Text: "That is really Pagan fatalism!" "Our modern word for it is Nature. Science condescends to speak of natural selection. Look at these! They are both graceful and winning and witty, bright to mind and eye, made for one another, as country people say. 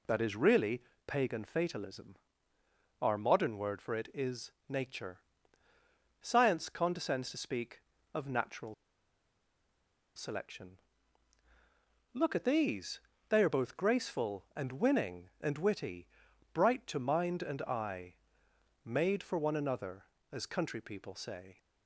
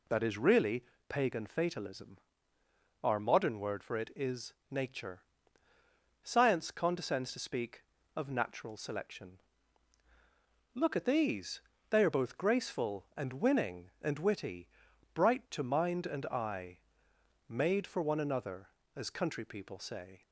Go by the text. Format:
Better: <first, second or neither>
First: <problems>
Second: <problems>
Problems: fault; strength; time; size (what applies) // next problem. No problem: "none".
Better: second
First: pauses between "really" and "Pagan"; slight; at 0.8 s; 0.24 s long // pauses between "is" and "Nature"; slight; at 4.5 s; 0.16 s long // pauses between "natural" and "selection"; strong; at 8.7 s; 1.4 s long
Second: pauses between "really" and "Pagan"; slight; at 0.8 s; 0.24 s long // pauses between "is" and "Nature"; slight; at 4.5 s; 0.16 s long